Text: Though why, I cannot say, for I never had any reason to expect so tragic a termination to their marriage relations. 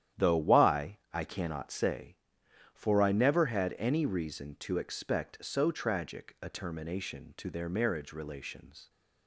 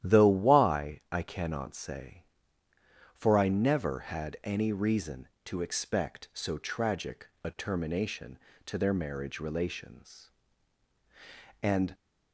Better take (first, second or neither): first